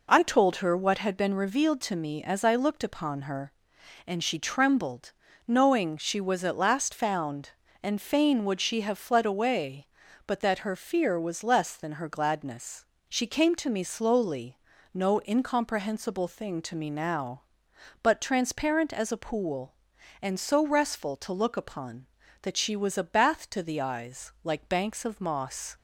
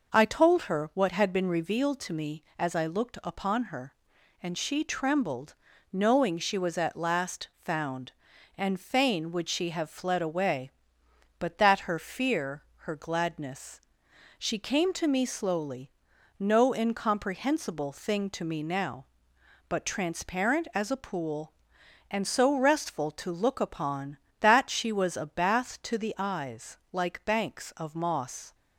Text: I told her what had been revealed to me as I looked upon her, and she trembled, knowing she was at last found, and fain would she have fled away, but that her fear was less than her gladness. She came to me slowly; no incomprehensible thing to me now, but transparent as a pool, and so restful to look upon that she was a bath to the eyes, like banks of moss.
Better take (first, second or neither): first